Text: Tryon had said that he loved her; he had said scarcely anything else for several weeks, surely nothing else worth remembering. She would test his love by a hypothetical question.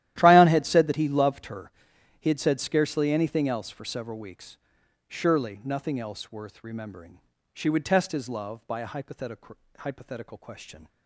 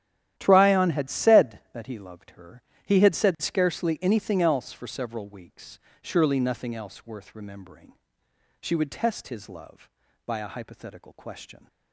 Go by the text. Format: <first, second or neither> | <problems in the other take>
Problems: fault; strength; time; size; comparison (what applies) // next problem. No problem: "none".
second | starts louder than the rest; strong; until 1.1 s; 13.5 dB; strong in the second // says "hypothetical" twice; at 9.7 s